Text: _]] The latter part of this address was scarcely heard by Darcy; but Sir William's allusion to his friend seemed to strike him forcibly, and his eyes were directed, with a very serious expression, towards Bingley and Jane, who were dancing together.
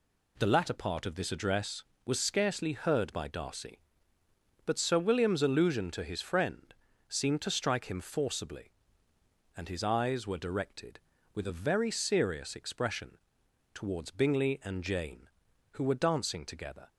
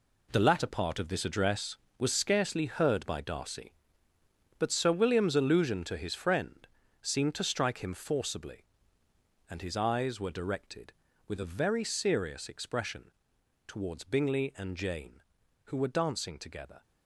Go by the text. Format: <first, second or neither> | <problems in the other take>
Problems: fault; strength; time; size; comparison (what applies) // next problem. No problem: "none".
first | gets quieter; strong; throughout; 11 dB // pauses between "friend" and "seemed"; slight; at 6.6 s; 0.34 s long; slight in the first